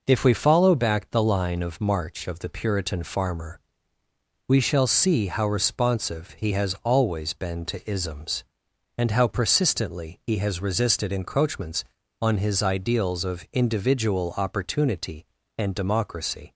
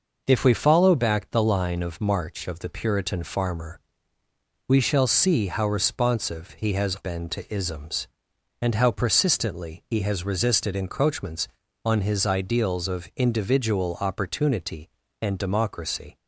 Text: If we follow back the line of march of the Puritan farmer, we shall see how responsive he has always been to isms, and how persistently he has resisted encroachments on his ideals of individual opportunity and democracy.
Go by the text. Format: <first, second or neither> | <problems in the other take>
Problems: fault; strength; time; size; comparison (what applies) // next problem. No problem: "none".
first | skips "always"; at 6.9 s